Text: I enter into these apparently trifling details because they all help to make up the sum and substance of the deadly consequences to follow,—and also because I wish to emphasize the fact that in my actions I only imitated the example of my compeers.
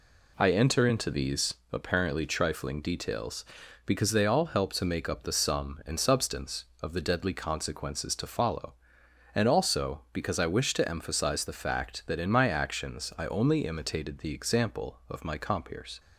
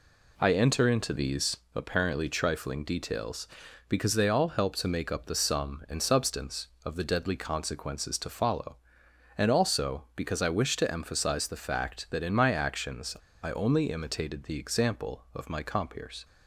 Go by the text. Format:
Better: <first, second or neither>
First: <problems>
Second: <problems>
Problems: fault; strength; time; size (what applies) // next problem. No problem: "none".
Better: first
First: pauses between "these" and "apparently"; slight; at 1.5 s; 0.18 s long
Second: pauses between "these" and "apparently"; slight; at 1.5 s; 0.18 s long // pauses between "actions" and "I"; slight; at 13.1 s; 0.27 s long